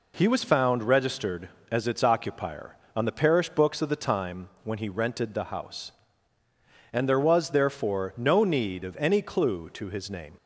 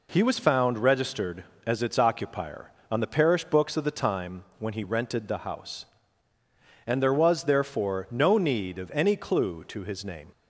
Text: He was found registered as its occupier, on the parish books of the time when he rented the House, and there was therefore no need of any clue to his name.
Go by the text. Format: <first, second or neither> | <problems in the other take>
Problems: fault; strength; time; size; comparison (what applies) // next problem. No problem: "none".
neither | pauses between "time" and "when"; slight; the same in both